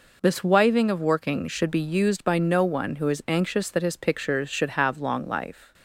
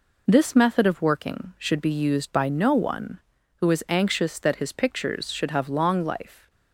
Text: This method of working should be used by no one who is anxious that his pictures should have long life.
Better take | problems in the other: second | says "wiving" for "method"; at 0.4 s

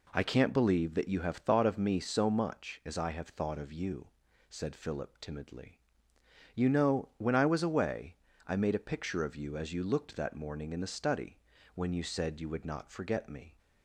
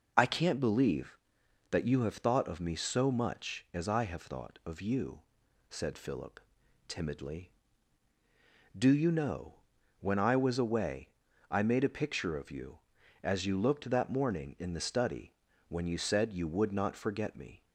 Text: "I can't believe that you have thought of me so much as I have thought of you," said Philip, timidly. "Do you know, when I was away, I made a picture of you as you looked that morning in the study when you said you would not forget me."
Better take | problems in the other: second | skips "Do"; at 6.1 s // pauses between "study" and "when"; slight; at 11.3 s; 0.34 s long; slight in the second

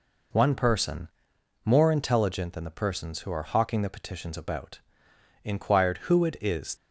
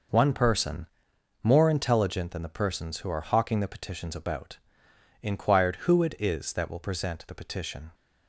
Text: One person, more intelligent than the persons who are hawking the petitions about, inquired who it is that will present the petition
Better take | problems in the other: second | stops before "that will present the petition"; at 6.7 s

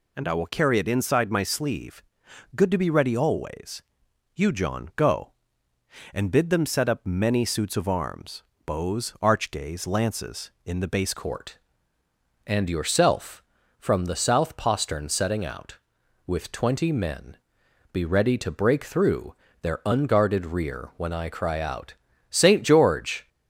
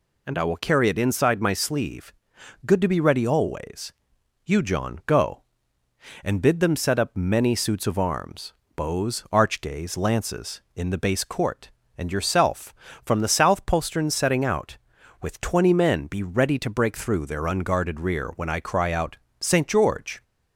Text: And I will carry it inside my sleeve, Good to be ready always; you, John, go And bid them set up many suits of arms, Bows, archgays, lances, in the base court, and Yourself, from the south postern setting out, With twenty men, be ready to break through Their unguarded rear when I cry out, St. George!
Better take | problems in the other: second | changes voice at "court"; from 11.1 s on; 12.1 s long // pauses between "through" and "Their"; slight; at 19.3 s; 0.26 s long

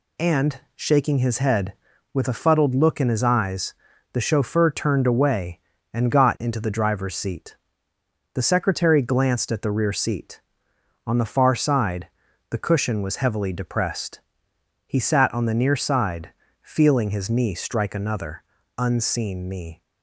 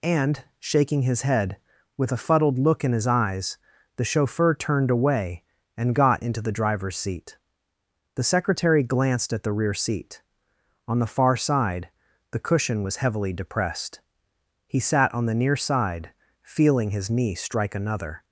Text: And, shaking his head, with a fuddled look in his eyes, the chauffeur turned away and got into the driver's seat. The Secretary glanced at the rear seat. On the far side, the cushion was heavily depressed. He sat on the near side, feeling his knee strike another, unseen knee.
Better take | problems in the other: first | stops before "unseen knee"; at 18.2 s

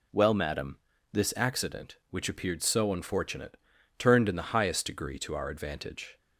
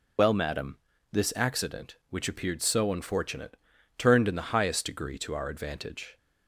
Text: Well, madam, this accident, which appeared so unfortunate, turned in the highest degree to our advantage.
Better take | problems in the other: first | loses the start of "Well"; at 0.1 s; 80 ms

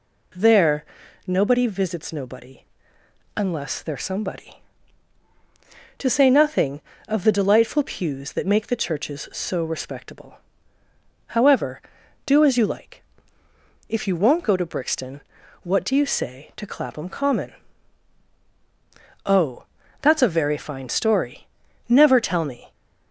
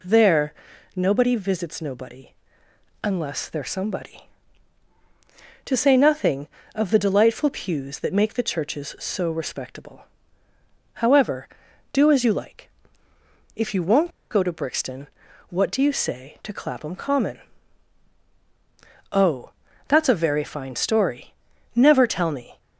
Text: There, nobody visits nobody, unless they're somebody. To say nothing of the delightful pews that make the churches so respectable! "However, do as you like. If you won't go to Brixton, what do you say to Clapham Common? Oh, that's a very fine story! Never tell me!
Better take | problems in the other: first | pauses between "won't" and "go"; slight; at 14.0 s; 0.21 s long

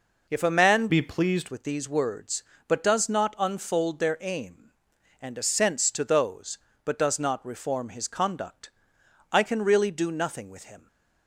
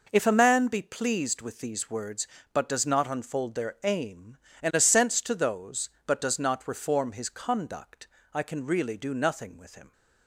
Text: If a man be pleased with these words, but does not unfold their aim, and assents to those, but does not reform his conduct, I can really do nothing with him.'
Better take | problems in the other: second | changes voice from "be" to "pleased"; from 0.8 to 1.4 s; 0.6 s long

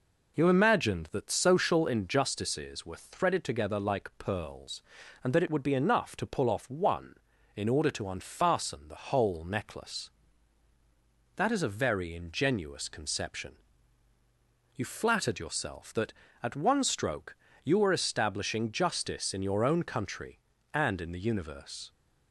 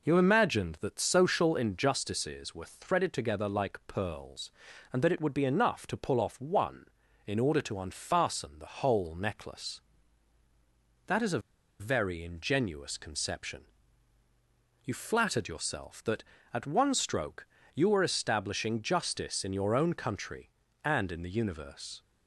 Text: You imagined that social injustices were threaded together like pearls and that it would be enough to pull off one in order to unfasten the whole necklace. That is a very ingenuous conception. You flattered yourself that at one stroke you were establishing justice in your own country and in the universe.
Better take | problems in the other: first | pauses between "a" and "very"; at 11.3 s; 0.40 s long // pauses between "stroke" and "you"; slight; at 17.4 s; 0.30 s long; slight in the first

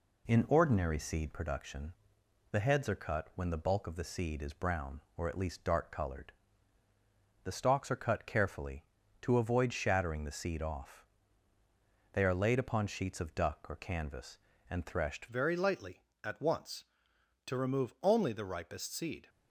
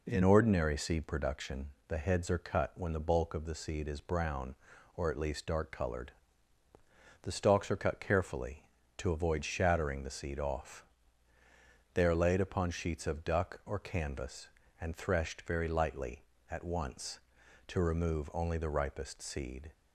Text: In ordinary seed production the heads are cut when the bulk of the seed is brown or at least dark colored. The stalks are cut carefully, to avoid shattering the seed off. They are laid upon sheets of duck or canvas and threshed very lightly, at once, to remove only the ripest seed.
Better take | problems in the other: second | pauses between "production" and "the"; noticeable; at 1.9 s; 0.58 s long; slight in the second // changes voice at "very"; from 15.2 s on; 4.0 s long

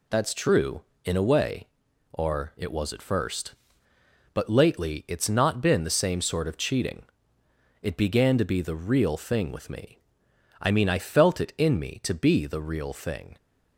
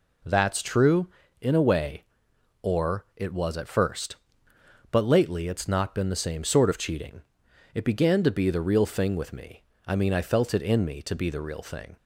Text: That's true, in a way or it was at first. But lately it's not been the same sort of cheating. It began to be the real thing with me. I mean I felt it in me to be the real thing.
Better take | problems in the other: neither | none

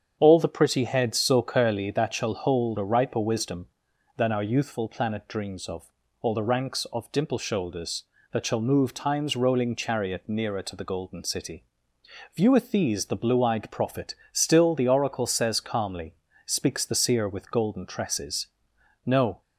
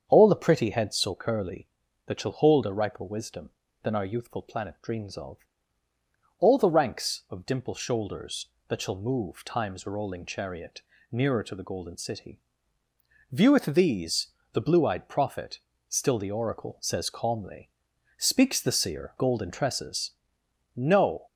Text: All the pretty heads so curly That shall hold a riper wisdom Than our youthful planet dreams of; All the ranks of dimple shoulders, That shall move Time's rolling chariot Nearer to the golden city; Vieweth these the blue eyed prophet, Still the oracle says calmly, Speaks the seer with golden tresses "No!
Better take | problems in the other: first | starts louder than the rest; strong; until 1.0 s; 7.5 dB; strong in the first // pauses between "chariot" and "Nearer"; slight; at 10.8 s; 0.28 s long // pauses between "these" and "the"; slight; at 14.2 s; 0.24 s long // skips "with"; at 19.1 s // pauses between "tresses" and "No"; noticeable; at 20.1 s; 0.62 s long; noticeable in the first

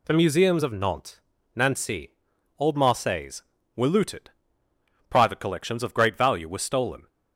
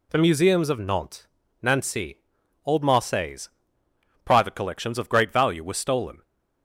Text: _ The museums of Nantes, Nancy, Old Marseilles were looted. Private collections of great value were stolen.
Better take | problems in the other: first | skips "were looted"; at 3.8 s

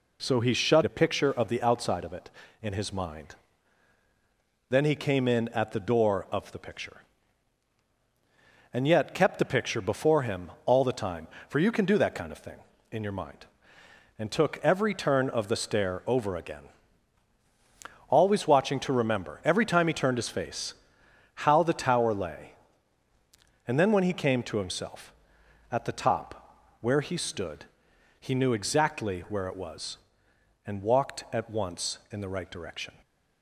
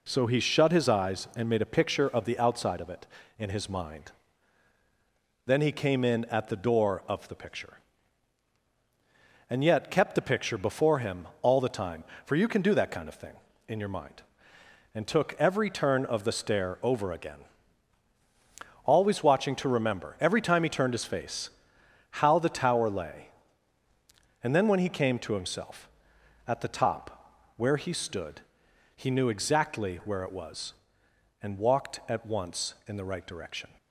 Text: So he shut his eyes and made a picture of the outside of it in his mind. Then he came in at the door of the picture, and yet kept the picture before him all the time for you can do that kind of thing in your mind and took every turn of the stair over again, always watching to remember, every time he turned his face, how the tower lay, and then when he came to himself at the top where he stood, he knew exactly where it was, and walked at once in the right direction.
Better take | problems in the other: second | skips "his eyes and made"; at 0.8 s // pauses between "top" and "where"; slight; at 26.5 s; 0.24 s long; slight in the second

